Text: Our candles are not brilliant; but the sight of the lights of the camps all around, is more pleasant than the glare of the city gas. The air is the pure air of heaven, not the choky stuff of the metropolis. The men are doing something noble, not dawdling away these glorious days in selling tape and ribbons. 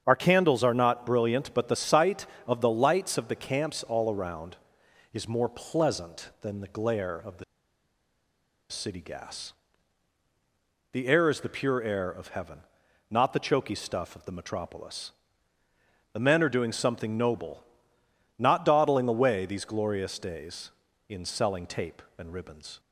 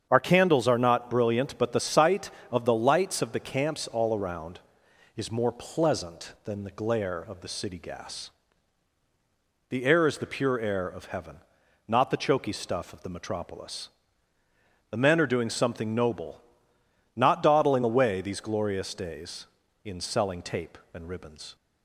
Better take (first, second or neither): second